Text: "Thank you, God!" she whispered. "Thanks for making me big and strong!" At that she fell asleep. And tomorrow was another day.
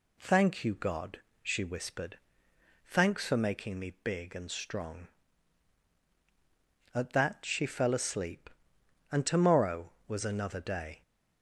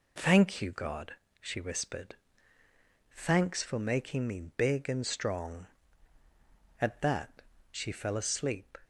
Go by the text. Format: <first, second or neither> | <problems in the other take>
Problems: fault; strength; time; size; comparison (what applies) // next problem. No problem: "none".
first | pauses between "me" and "big"; slight; at 4.4 s; 0.16 s long // pauses between "that" and "she"; slight; at 7.4 s; 0.28 s long // stops before "And tomorrow was another day"; at 8.8 s